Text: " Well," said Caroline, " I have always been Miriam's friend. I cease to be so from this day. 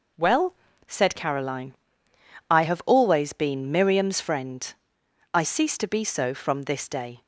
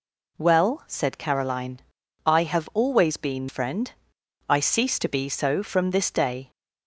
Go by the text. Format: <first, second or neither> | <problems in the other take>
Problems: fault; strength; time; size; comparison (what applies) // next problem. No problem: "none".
first | skips "Miriam's"; at 3.4 s